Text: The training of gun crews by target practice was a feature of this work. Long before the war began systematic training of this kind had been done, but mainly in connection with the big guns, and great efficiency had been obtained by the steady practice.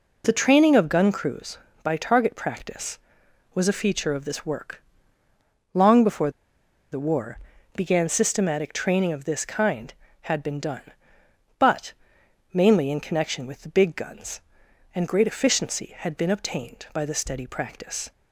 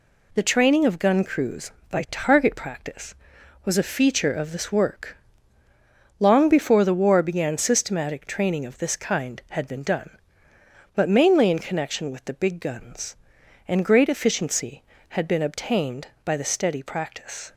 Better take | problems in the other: second | pauses between "before" and "the"; noticeable; at 6.3 s; 0.60 s long // pauses between "war" and "began"; slight; at 7.3 s; 0.36 s long // pauses between "but" and "mainly"; noticeable; at 11.9 s; 0.60 s long

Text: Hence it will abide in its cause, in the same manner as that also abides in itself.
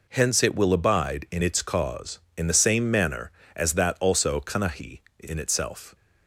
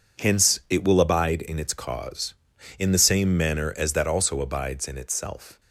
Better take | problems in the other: second | says "kanahi" for "abides"; at 4.4 s

